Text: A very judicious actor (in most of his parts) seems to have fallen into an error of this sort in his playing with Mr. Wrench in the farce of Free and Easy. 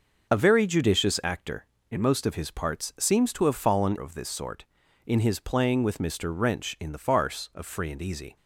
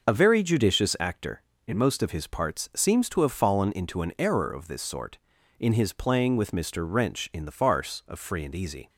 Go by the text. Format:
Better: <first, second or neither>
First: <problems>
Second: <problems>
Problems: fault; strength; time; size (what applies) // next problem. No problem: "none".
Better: second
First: starts louder than the rest; until 1.3 s; 6.5 dB // skips "into an error"; at 3.9 s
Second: starts louder than the rest; until 1.1 s; 6.5 dB